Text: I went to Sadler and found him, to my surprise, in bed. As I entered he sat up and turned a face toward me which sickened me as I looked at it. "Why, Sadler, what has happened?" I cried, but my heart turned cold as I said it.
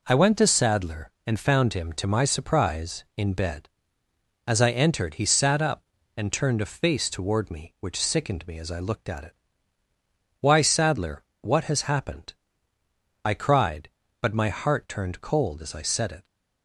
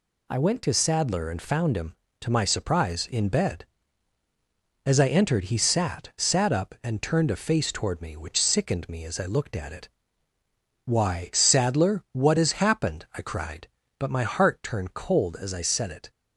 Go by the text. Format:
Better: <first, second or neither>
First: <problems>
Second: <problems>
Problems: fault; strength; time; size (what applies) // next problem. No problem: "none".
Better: first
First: none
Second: says "sat" twice; at 6.1 s